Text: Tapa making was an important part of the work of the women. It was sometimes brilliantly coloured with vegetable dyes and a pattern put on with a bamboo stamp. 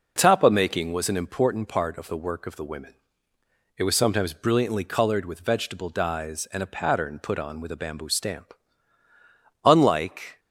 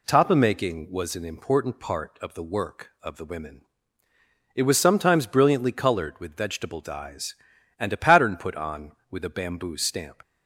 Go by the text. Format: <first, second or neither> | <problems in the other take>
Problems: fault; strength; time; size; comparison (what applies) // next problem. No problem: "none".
second | goes on to say "Unlike"; noticeable; from 9.6 s on; 0.76 s long